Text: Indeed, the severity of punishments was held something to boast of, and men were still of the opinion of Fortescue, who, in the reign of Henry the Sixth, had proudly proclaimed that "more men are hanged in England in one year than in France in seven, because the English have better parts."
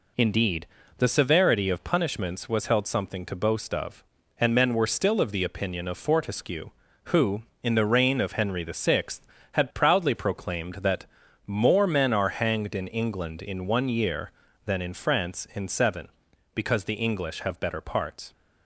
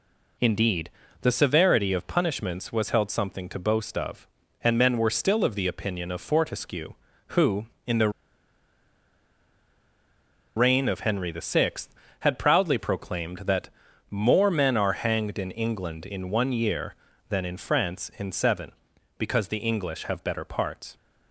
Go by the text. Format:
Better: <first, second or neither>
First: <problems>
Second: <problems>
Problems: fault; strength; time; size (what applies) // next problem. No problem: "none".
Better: first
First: pauses between "that" and "more"; at 11.0 s; 0.42 s long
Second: pauses between "the" and "reign"; strong; at 8.0 s; 2.4 s long // pauses between "that" and "more"; at 13.6 s; 0.42 s long